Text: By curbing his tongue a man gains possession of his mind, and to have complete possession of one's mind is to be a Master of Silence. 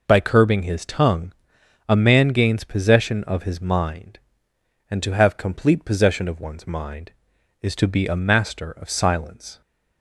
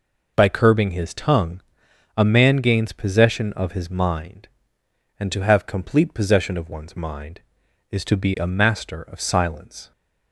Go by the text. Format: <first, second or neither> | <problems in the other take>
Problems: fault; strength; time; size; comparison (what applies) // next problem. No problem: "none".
neither | pauses between "tongue" and "a"; noticeable; the same in both